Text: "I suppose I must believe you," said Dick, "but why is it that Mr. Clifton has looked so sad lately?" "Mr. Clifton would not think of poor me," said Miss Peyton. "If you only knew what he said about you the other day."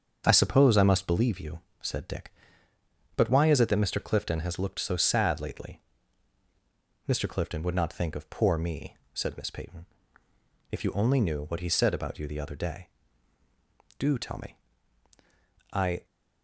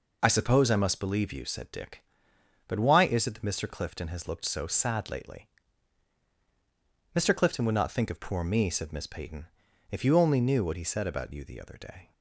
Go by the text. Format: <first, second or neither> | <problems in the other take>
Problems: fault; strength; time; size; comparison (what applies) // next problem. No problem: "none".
second | starts louder than the rest; strong; until 1.2 s; 7 dB // goes on to say "Do tell me I"; strong; from 13.9 s on; 2.0 s long